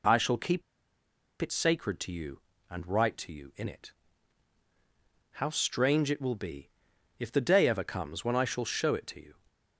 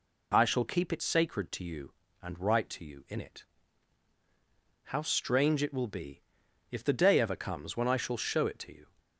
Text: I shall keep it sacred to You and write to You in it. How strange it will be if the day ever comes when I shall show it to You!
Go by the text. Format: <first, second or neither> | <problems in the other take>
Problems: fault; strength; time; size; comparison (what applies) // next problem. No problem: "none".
second | pauses between "keep" and "it"; noticeable; at 0.6 s; 0.78 s long // pauses between "be" and "if"; noticeable; at 6.7 s; 0.50 s long; noticeable in the second